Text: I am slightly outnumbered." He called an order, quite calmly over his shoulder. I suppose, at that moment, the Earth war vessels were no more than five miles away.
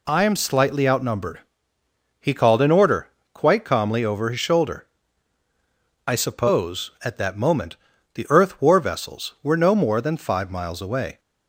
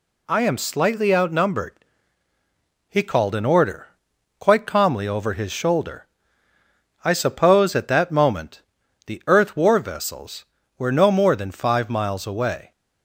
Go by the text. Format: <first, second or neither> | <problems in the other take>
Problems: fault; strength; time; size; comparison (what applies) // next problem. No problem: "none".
neither | none